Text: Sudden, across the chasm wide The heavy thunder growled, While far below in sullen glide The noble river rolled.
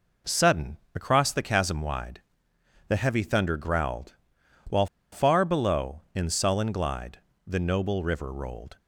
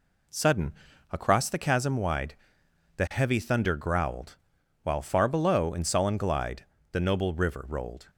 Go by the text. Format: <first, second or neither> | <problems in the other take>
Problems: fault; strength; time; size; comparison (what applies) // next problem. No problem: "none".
second | pauses between "wide" and "The"; noticeable; at 2.1 s; 0.68 s long; noticeable in the second // pauses between "While" and "far"; slight; at 4.8 s; 0.24 s long // pauses between "glide" and "The"; slight; at 7.1 s; 0.26 s long; slight in the second